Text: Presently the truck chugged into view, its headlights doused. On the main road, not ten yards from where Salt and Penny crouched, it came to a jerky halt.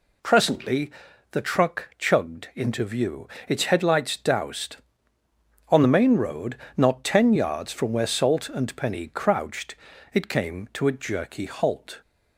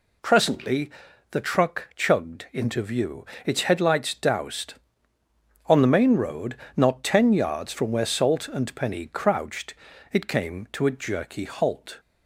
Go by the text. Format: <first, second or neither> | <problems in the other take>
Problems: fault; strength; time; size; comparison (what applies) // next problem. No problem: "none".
neither | pauses between "Presently" and "the"; the same in both